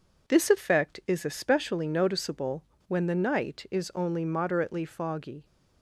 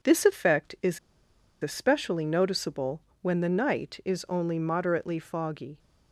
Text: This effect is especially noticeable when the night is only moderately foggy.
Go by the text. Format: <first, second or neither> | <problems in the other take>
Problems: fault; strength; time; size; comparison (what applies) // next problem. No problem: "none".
first | pauses between "is" and "especially"; noticeable; at 0.9 s; 0.65 s long // pauses between "noticeable" and "when"; slight; at 3.0 s; 0.20 s long; slight in the first